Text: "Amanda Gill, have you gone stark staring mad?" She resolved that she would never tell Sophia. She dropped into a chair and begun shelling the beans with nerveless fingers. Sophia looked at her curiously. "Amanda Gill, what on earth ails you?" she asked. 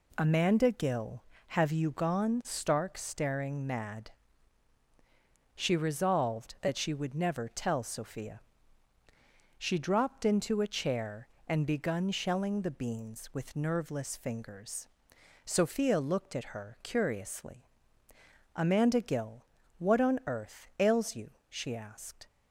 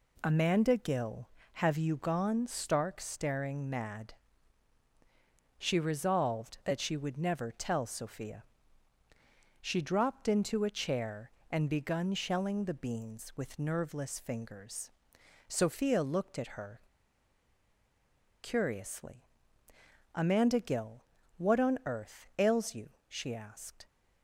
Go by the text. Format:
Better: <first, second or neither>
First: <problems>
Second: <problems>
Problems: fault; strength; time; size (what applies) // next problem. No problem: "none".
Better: first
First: none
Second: pauses between "her" and "curiously"; strong; at 16.8 s; 1.6 s long